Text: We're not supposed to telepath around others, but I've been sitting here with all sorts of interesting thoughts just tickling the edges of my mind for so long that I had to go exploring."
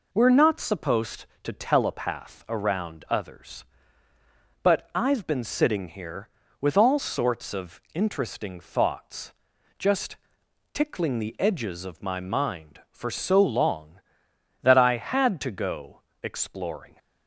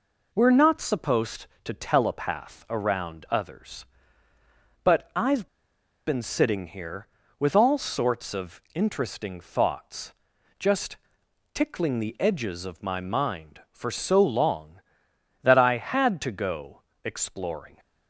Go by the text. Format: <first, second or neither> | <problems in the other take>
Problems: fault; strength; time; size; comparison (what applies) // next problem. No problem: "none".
first | pauses between "I've" and "been"; noticeable; at 5.4 s; 0.60 s long // pauses between "thoughts" and "just"; at 10.1 s; 0.44 s long; also in the first // pauses between "just" and "tickling"; noticeable; at 10.9 s; 0.58 s long; noticeable in the first // pauses between "go" and "exploring"; slight; at 16.8 s; 0.22 s long; slight in the first